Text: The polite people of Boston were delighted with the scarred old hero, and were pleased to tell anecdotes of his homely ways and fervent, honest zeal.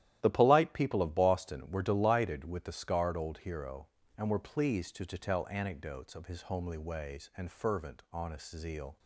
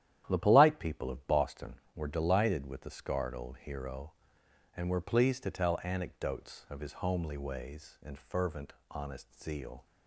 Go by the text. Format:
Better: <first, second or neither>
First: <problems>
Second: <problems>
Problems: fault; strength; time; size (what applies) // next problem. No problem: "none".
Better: second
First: starts louder than the rest; strong; until 1.2 s; 12.5 dB // says "to" twice; at 5.0 s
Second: starts louder than the rest; strong; until 1.2 s; 11 dB